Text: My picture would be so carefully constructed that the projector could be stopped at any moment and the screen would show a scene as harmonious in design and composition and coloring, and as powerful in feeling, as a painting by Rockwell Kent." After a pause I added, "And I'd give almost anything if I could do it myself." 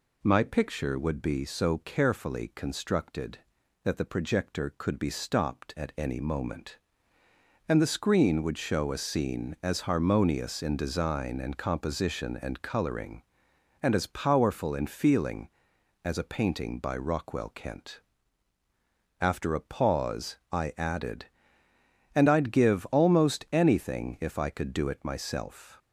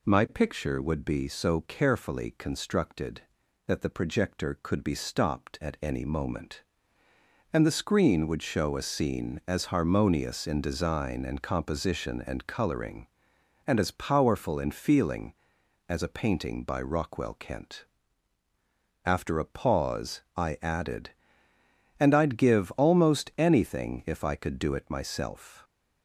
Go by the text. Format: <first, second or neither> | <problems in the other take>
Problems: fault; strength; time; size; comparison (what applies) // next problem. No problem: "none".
neither | none